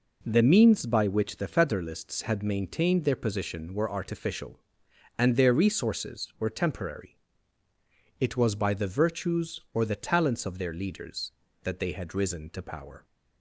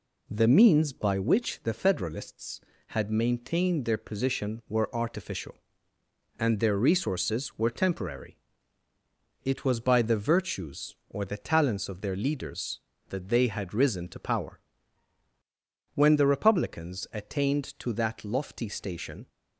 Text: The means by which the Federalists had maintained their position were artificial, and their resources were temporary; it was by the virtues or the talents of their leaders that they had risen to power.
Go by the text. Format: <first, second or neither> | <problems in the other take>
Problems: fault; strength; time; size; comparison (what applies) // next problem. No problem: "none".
first | goes on to say "When the Republicans attained to that lofty station"; strong; from 15.9 s on; 3.3 s long